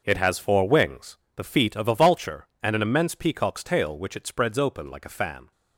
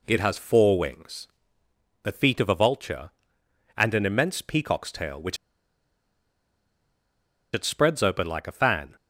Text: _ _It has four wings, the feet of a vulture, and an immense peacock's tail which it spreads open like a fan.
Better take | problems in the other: first | pauses between "which" and "it"; strong; at 5.3 s; 2.1 s long

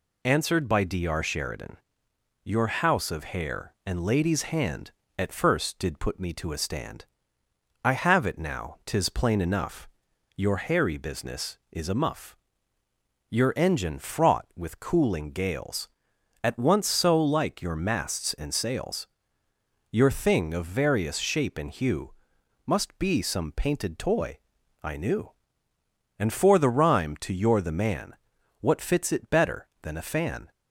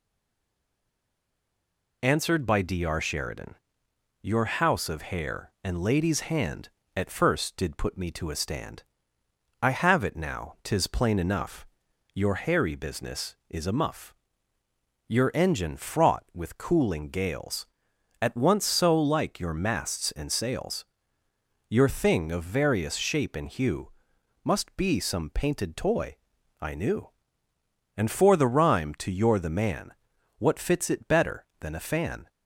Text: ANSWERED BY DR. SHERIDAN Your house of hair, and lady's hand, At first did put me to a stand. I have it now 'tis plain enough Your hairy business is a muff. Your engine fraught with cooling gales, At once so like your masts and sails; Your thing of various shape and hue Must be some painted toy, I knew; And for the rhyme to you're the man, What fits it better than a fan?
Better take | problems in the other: first | stays silent before the first word; noticeable; until 2.0 s; 2.0 s long // pauses between "SHERIDAN" and "Your"; noticeable; at 3.5 s; 0.66 s long; noticeable in the first // pauses between "enough" and "Your"; noticeable; at 11.6 s; 0.48 s long; noticeable in the first // pauses between "hue" and "Must"; noticeable; at 23.9 s; 0.54 s long; noticeable in the first

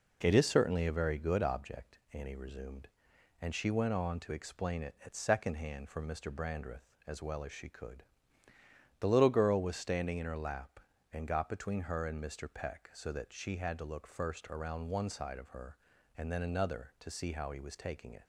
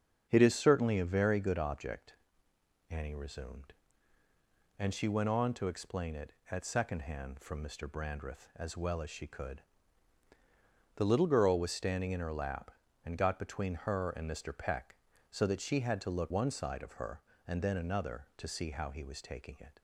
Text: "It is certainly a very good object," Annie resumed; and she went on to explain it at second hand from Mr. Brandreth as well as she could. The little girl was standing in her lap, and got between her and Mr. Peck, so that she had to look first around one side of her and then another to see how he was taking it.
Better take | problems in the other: first | starts louder than the rest; until 1.3 s; 7 dB // skips "first around"; at 16.3 s

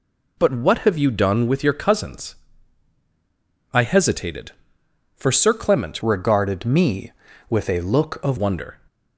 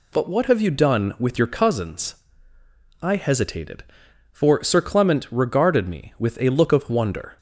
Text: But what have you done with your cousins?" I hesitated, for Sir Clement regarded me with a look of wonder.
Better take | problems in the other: second | changes voice from "regarded" to "of"; from 6.0 to 8.3 s; 2.3 s long

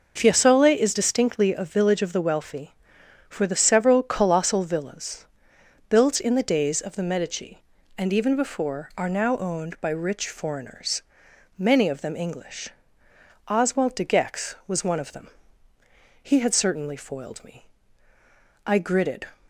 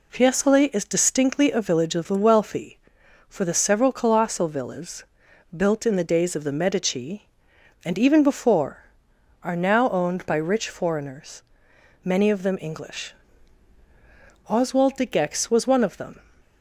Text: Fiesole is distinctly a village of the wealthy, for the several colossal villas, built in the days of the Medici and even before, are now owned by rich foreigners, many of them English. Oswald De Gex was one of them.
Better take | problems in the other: second | goes on to say "He had certainly foiled me I gritted"; strong; from 16.2 s on; 3.0 s long

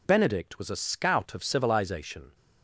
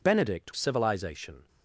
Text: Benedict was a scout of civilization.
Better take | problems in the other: first | skips "was a scout of"; at 0.5 s

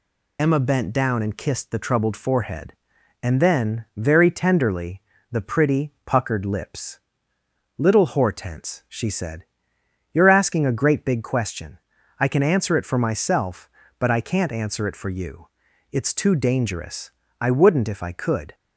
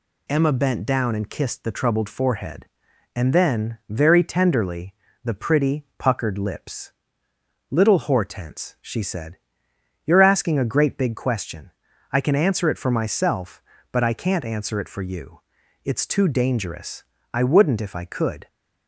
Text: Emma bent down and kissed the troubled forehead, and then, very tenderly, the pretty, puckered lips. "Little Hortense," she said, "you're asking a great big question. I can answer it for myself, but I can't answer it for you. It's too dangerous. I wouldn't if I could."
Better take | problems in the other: second | loses the start of "Emma"; at 0.3 s; 35 ms

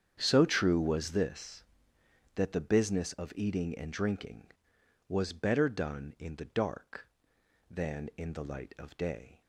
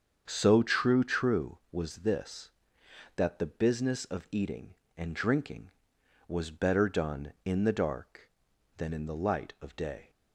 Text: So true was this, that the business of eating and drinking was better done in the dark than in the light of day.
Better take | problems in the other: first | starts louder than the rest; strong; until 1.2 s; 7 dB; strong in the first // says "true" twice; at 1.0 s

